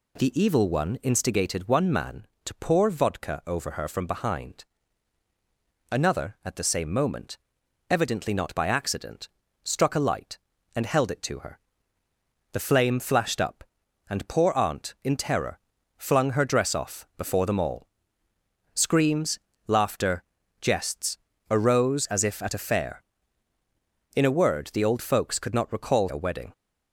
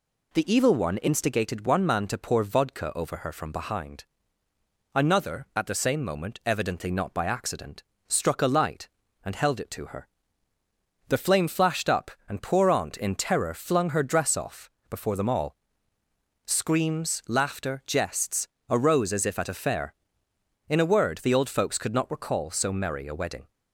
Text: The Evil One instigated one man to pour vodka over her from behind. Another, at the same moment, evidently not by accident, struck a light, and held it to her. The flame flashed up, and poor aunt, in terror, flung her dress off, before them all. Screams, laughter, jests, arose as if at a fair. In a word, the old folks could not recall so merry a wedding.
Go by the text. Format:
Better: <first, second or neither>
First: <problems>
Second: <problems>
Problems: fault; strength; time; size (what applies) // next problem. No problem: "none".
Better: second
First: skips "so merry"; at 26.0 s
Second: none